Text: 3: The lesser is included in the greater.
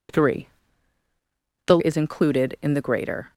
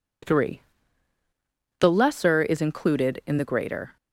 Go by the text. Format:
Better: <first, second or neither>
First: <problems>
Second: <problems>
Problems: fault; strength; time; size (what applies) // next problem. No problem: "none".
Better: second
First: skips "lesser"; at 1.7 s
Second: none